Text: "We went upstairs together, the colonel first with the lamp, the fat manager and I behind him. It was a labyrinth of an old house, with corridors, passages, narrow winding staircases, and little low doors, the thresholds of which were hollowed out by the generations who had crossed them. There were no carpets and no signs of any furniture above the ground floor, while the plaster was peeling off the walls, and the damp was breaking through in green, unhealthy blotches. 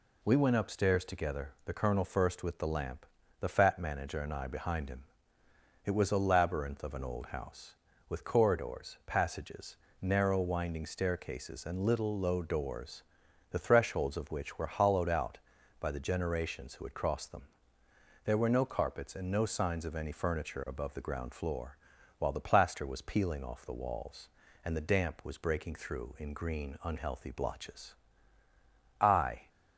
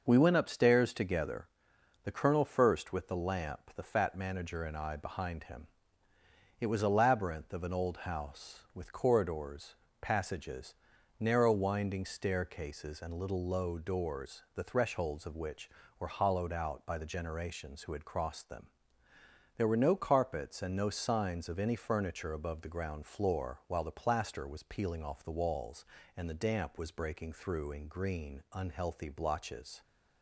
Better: second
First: goes on to say "I"; slight; from 29.0 s on; 0.46 s long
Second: none

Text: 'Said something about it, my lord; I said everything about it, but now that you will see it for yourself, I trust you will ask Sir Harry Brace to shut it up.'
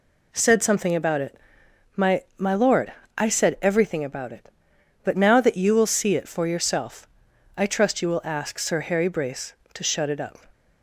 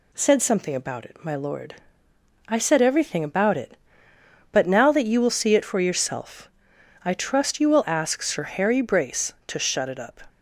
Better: second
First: says "my" twice; at 2.3 s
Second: none

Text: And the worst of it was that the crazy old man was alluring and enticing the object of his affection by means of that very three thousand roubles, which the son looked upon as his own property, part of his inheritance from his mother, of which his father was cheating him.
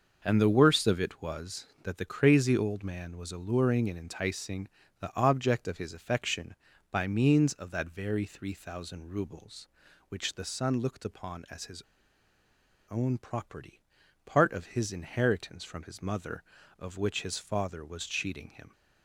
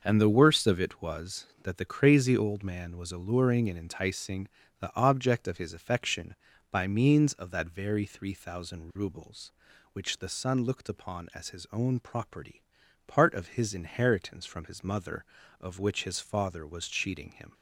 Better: second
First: starts louder than the rest; noticeable; until 1.2 s; 6 dB // pauses between "enticing" and "the"; slight; at 4.6 s; 0.32 s long // pauses between "his" and "own"; at 11.8 s; 1.0 s long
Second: starts louder than the rest; noticeable; until 1.0 s; 6 dB // pauses between "enticing" and "the"; slight; at 4.4 s; 0.32 s long

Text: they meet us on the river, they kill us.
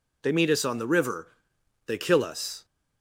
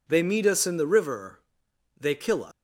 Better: first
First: none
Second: says "in" for "on"; at 0.6 s

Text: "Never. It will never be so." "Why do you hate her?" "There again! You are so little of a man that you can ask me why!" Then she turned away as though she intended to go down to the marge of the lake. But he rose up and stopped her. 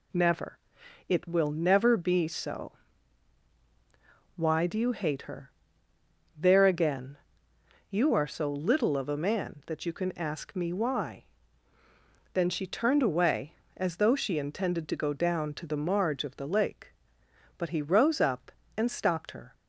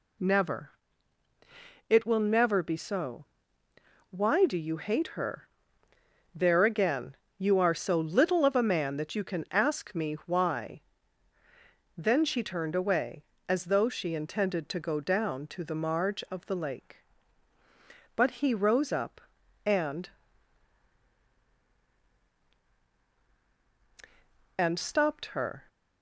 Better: first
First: none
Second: says "and" twice; at 24.5 s

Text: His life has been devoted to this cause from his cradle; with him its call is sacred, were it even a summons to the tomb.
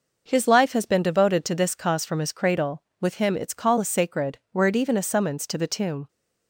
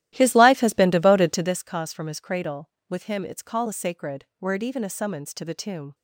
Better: first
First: none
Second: starts louder than the rest; strong; until 1.6 s; 14 dB

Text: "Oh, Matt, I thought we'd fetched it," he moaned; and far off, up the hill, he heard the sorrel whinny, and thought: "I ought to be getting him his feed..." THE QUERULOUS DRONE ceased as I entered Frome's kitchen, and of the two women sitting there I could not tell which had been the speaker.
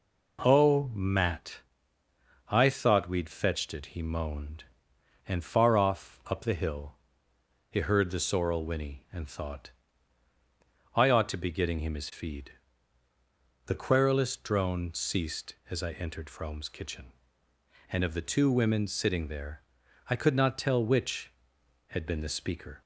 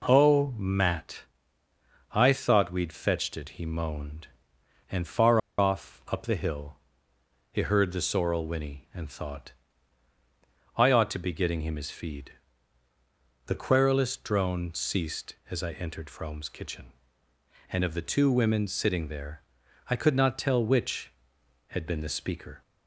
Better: first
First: pauses between "there" and "I"; noticeable; at 19.6 s; 0.48 s long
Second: pauses between "far" and "off"; slight; at 5.3 s; 0.19 s long // pauses between "there" and "I"; noticeable; at 19.4 s; 0.48 s long

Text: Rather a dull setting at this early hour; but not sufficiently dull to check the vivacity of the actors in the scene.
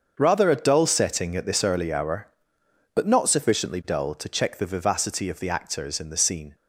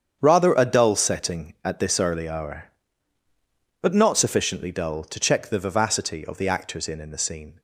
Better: first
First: starts louder than the rest; until 1.1 s; 6.5 dB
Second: starts louder than the rest; strong; until 1.2 s; 8 dB // says "in" twice; at 6.9 s

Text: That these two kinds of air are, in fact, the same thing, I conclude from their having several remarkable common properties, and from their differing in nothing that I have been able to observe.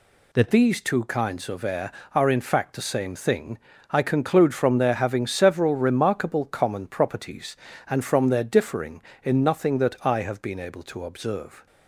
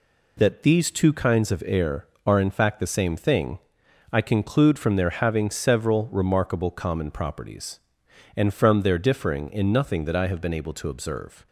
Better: second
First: changes voice at "these"; from 0.5 s on; 11.1 s long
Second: none

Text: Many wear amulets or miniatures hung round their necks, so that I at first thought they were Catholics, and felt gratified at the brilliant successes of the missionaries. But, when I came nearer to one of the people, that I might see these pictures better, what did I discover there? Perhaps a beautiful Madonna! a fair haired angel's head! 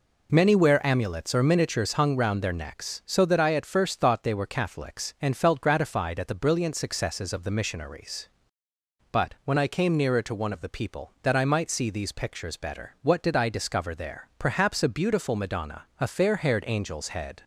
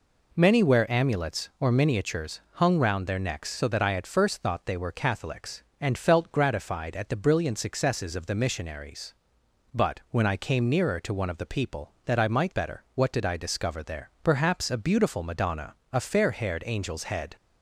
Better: first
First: none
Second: skips "see these pictures"; at 12.5 s

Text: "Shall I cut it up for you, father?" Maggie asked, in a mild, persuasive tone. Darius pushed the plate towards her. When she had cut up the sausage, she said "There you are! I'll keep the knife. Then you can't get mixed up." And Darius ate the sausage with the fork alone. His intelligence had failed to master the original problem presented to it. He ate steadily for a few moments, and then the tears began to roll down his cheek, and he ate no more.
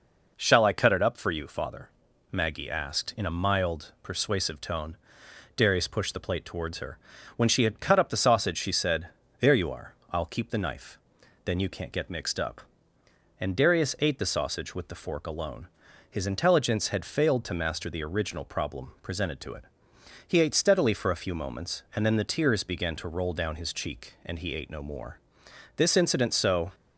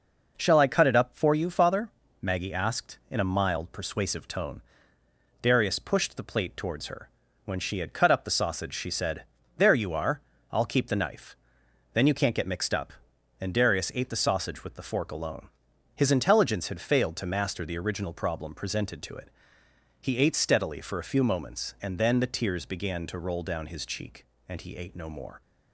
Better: second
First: pauses between "said" and "There"; slight; at 9.0 s; 0.32 s long // goes on to say "This incident so"; noticeable; from 25.7 s on; 0.96 s long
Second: pauses between "said" and "There"; slight; at 9.2 s; 0.32 s long

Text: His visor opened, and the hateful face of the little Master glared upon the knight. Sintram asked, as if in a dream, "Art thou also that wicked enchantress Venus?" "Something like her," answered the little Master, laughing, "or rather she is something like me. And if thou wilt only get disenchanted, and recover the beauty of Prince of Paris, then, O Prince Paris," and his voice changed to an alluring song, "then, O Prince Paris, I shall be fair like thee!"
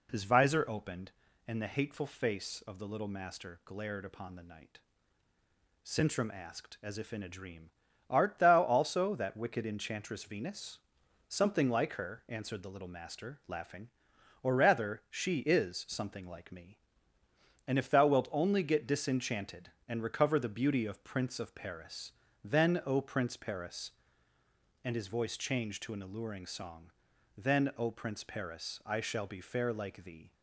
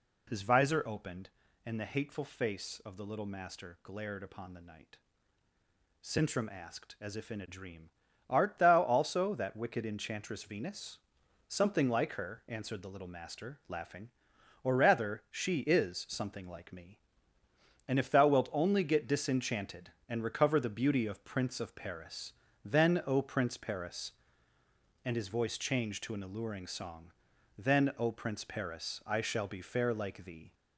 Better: first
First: none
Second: gets louder; throughout; 3.5 dB

